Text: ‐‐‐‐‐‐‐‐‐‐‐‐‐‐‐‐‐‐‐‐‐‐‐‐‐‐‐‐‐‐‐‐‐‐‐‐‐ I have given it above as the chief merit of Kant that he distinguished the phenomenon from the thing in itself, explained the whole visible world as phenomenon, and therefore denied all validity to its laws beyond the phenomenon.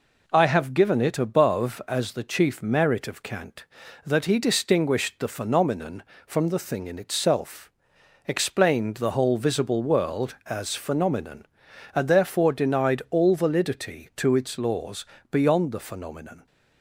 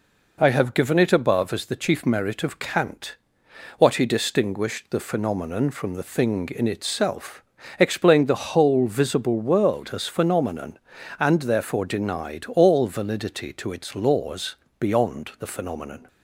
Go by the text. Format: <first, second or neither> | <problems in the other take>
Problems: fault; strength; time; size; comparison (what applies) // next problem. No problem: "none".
first | says "what" for "that"; at 3.7 s // pauses between "laws" and "beyond"; slight; at 14.5 s; 0.24 s long; slight in the first